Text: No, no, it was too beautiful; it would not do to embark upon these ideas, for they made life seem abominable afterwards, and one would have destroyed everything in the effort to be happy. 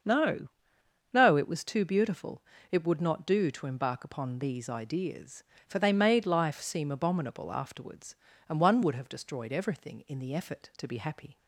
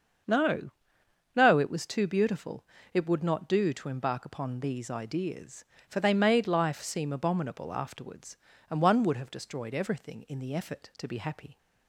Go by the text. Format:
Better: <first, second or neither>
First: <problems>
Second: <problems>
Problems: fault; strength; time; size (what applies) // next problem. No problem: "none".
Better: neither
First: starts louder than the rest; until 1.6 s; 6.5 dB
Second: starts louder than the rest; until 1.9 s; 6.5 dB